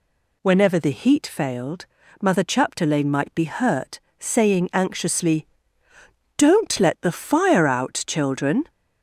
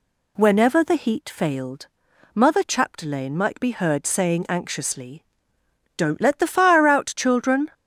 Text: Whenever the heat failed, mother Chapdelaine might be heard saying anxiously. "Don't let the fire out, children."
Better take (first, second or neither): second